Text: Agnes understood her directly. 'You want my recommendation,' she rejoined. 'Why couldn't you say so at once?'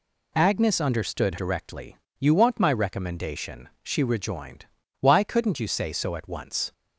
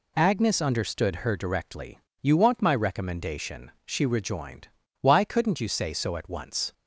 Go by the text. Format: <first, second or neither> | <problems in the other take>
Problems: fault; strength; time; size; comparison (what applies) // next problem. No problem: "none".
second | skips "her"; at 1.3 s